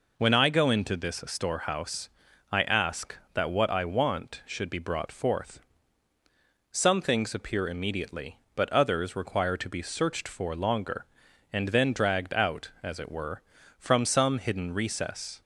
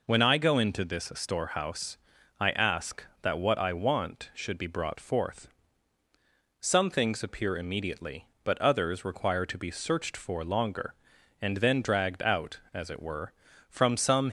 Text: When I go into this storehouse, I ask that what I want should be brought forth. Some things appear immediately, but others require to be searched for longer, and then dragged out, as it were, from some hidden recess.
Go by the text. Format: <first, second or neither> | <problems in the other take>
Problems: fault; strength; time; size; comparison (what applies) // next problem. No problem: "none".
first | stops before "hidden recess"; at 14.2 s